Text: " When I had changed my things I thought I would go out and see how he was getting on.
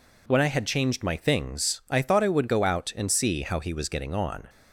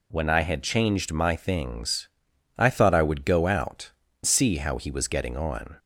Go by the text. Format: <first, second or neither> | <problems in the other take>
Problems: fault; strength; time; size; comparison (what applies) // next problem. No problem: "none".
first | pauses between "things" and "I"; noticeable; at 2.0 s; 0.48 s long // skips "and"; at 4.0 s